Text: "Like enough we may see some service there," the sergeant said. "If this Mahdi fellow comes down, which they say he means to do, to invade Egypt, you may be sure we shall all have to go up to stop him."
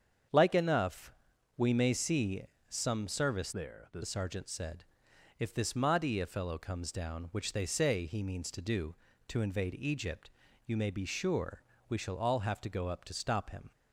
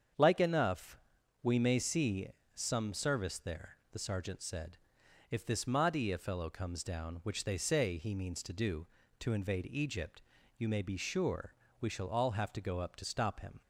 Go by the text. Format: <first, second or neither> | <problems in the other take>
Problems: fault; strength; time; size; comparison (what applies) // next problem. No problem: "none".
second | starts louder than the rest; strong; until 1.7 s; 7.5 dB; strong in the second // pauses between "enough" and "we"; noticeable; at 1.1 s; 0.46 s long; noticeable in the second // pauses between "see" and "some"; slight; at 2.4 s; 0.26 s long; slight in the second // changes voice from "there" to "the"; from 3.5 to 4.0 s; 0.5 s long // pauses between "sure" and "we"; slight; at 11.6 s; 0.26 s long; slight in the second